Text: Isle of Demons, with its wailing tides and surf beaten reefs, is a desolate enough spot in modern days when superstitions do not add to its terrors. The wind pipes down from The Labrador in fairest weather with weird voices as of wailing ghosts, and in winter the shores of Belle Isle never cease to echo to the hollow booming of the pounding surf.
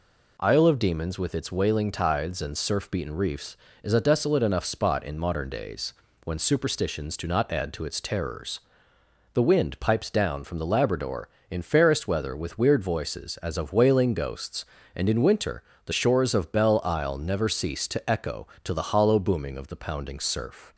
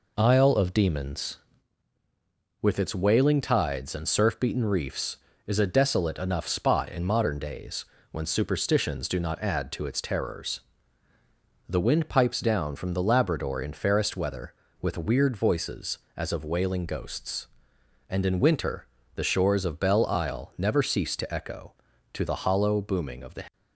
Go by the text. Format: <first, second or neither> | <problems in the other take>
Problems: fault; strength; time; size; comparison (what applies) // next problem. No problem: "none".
first | pauses between "days" and "when"; slight; at 7.8 s; 0.26 s long; slight in the first // pauses between "winter" and "the"; slight; at 18.8 s; 0.30 s long; slight in the first // stops before "pounding surf"; at 23.5 s